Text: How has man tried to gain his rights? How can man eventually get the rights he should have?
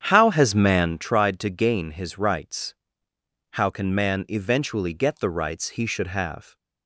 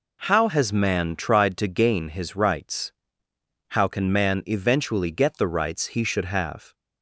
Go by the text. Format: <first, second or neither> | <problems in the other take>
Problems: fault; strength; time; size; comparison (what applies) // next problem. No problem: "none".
second | starts louder than the rest; strong; until 0.9 s; 8.5 dB